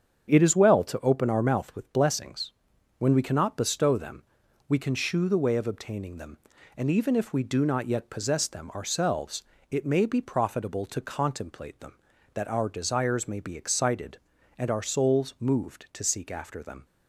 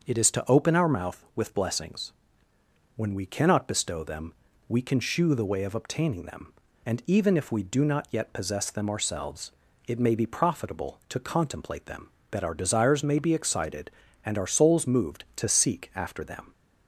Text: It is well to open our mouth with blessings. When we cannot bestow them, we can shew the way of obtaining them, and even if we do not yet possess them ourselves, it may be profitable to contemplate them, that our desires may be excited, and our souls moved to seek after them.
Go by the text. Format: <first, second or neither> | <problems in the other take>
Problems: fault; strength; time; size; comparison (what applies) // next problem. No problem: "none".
first | starts louder than the rest; until 1.1 s; 6.5 dB; strong in the first // skips "well"; at 0.3 s